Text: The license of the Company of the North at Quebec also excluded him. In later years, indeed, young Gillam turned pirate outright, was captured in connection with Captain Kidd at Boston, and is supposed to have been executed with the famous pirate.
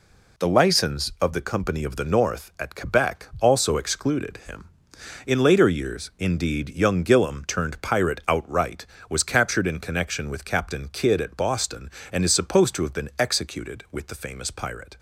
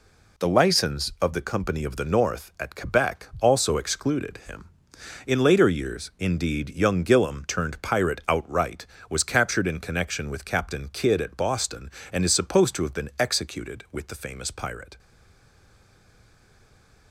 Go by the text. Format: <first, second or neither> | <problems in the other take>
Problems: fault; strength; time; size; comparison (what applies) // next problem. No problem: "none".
first | stays silent after the last word; from 14.9 s on; 2.2 s long